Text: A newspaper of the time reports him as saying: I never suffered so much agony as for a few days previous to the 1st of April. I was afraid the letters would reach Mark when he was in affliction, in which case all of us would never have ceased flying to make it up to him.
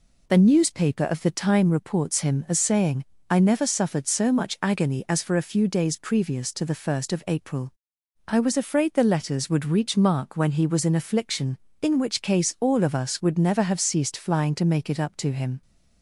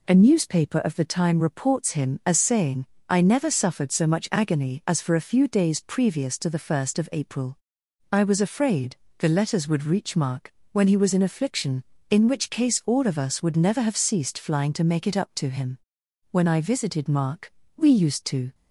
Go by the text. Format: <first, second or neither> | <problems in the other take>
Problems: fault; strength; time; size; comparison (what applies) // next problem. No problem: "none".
first | pauses between "afraid" and "the"; slight; at 8.9 s; 0.24 s long // pauses between "Mark" and "when"; slight; at 10.5 s; 0.20 s long // goes on to say "When I visited Mark we used to"; strong; from 16.3 s on; 2.2 s long